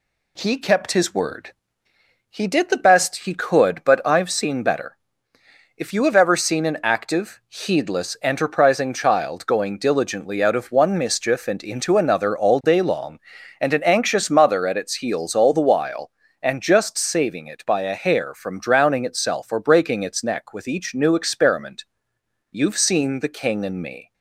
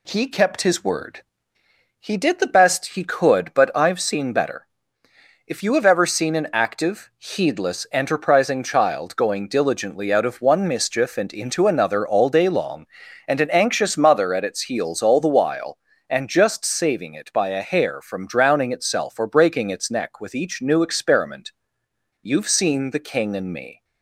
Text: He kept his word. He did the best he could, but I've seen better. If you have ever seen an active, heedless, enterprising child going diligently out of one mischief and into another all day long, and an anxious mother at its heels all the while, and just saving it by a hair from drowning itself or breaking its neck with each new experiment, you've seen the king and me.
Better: neither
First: none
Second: none

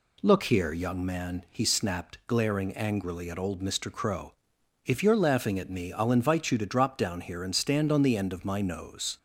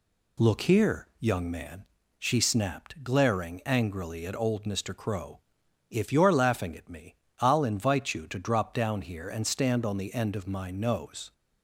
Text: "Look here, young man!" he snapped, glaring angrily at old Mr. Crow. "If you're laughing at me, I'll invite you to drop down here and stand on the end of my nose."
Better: first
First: none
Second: says "she" for "he"; at 2.1 s

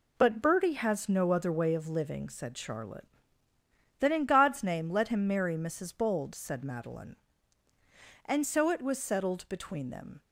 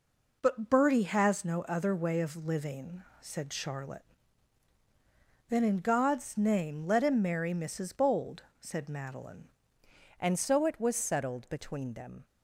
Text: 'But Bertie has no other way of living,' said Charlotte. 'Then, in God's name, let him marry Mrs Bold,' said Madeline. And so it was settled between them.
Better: first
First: none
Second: changes voice at "And"; from 10.2 s on; 2.0 s long

